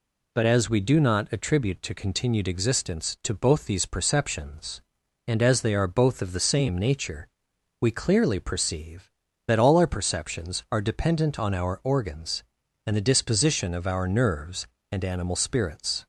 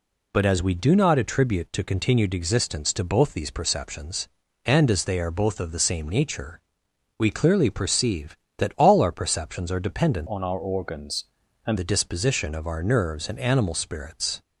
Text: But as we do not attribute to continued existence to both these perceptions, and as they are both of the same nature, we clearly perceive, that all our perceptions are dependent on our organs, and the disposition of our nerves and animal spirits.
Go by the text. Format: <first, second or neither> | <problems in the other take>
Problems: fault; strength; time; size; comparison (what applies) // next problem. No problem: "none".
first | changes voice from "on" to "and"; from 10.2 to 11.7 s; 1.5 s long